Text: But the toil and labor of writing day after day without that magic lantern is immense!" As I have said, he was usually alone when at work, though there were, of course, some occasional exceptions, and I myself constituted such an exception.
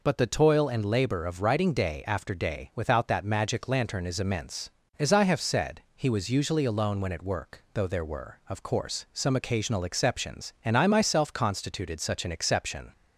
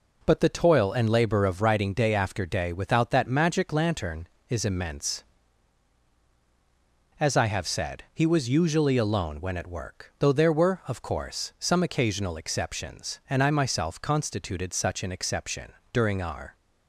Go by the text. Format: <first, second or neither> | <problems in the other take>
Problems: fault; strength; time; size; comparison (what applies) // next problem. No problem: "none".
first | goes on to say "During our"; noticeable; from 15.9 s on; 0.62 s long